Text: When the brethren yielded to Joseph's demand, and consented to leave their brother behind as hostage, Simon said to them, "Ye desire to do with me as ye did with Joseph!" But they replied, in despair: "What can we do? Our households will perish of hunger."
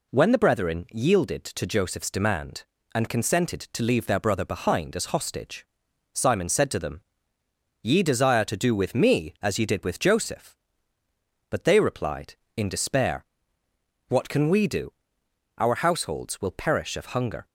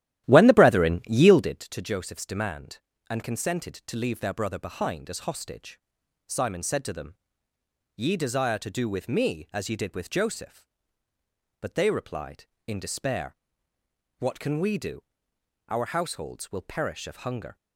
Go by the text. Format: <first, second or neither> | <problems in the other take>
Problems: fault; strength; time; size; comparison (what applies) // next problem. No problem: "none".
first | starts louder than the rest; strong; until 1.7 s; 13 dB